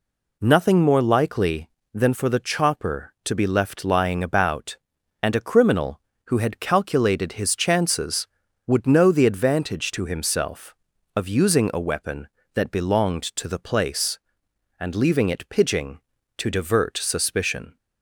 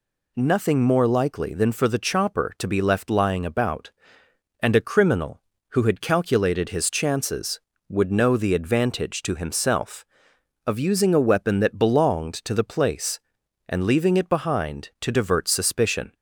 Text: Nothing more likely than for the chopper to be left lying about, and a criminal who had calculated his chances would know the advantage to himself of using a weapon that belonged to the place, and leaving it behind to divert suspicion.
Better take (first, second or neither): second